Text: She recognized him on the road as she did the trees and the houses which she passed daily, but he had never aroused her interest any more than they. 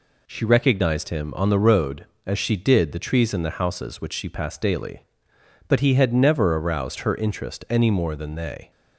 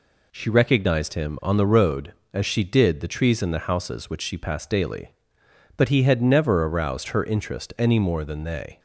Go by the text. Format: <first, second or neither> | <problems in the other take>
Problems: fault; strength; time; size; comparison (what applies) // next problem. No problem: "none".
neither | none